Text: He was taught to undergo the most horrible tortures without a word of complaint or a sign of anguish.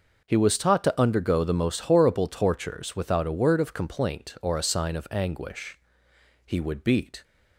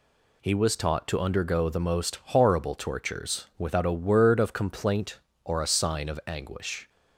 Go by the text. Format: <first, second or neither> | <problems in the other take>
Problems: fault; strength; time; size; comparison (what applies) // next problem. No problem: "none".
second | goes on to say "He would beat"; noticeable; from 6.4 s on; 0.78 s long